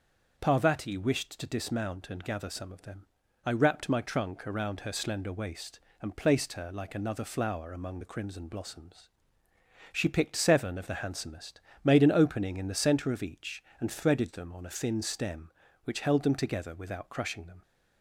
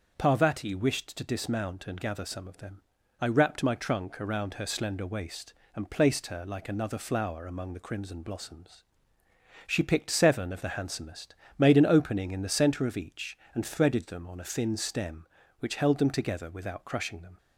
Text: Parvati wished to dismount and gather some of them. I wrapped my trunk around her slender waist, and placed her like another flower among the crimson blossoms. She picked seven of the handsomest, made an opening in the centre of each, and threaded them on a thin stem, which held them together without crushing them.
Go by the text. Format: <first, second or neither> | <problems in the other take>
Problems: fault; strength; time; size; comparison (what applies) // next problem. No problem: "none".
neither | starts louder than the rest; the same in both